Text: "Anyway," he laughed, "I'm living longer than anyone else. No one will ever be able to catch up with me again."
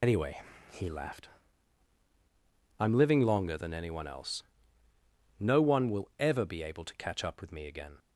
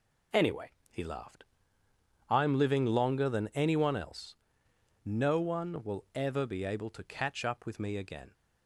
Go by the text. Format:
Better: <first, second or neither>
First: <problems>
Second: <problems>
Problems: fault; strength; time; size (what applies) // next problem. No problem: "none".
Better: second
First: loses the start of "Anyway"; at 0.0 s; 85 ms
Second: none